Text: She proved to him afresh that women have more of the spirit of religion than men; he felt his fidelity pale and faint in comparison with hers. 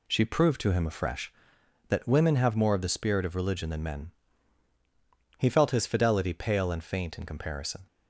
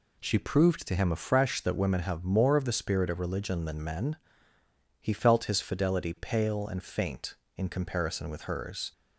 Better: second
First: stops before "with hers"; at 7.8 s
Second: none

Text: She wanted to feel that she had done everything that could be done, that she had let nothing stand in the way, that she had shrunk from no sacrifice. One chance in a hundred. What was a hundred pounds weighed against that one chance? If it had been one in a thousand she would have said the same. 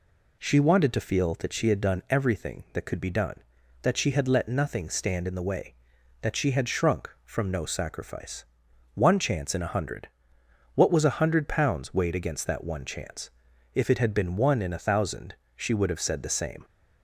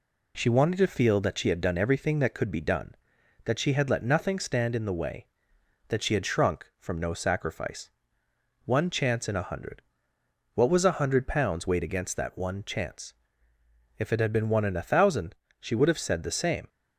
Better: neither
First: pauses between "thousand" and "she"; slight; at 15.3 s; 0.22 s long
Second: pauses between "thousand" and "she"; slight; at 15.3 s; 0.24 s long

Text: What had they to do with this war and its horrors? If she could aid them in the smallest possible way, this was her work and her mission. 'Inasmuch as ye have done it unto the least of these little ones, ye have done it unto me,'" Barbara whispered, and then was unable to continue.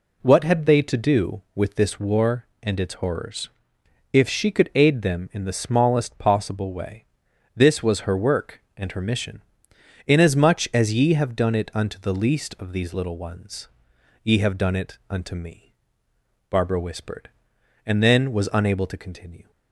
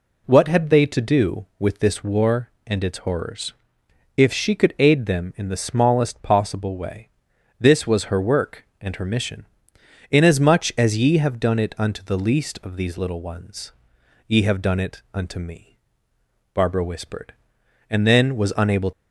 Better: first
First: none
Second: stops before "to continue"; at 18.9 s

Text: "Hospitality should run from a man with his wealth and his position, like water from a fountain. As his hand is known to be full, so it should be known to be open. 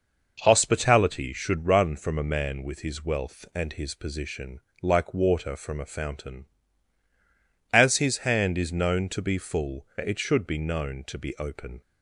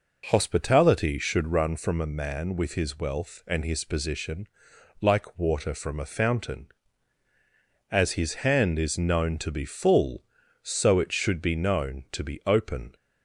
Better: second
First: skips "so"; at 9.9 s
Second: none

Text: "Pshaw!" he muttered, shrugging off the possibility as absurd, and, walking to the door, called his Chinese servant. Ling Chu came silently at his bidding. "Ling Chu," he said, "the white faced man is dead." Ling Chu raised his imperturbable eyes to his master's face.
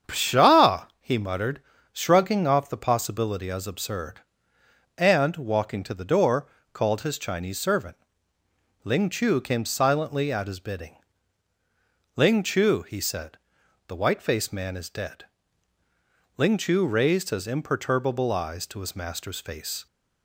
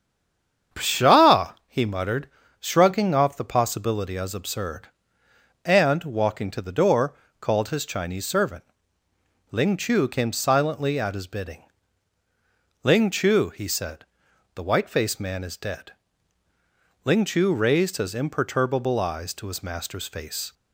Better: first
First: starts louder than the rest; strong; until 1.2 s; 8 dB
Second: stays silent before the first word; slight; until 0.7 s; 0.7 s long // starts louder than the rest; strong; until 1.8 s; 8 dB

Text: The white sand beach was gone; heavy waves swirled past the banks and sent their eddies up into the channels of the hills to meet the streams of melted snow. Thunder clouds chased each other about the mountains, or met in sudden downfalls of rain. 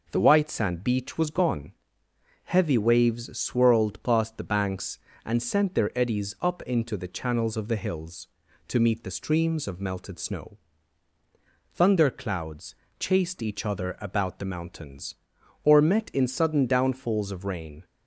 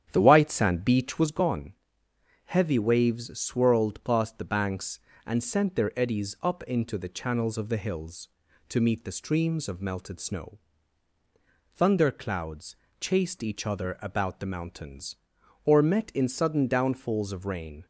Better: first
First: pauses between "clouds" and "chased"; slight; at 12.7 s; 0.24 s long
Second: starts louder than the rest; strong; until 1.3 s; 9.5 dB // pauses between "clouds" and "chased"; slight; at 12.7 s; 0.24 s long

